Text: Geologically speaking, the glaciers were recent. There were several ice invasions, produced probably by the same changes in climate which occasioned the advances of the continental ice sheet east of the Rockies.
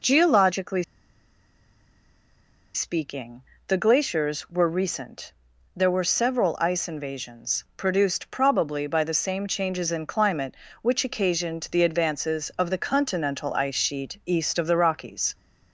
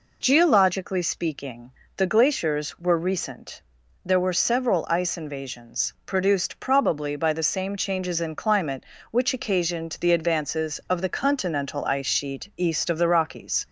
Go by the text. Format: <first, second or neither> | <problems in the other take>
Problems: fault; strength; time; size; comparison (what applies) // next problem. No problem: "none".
second | pauses between "Geologically" and "speaking"; strong; at 0.8 s; 1.9 s long